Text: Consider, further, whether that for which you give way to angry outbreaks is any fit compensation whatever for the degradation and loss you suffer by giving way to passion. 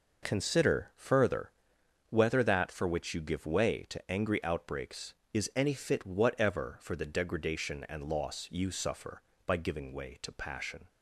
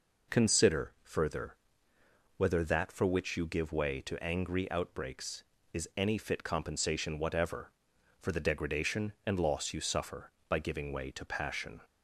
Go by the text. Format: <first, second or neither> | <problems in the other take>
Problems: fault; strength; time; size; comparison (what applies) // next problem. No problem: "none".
second | skips "compensation"; at 6.0 s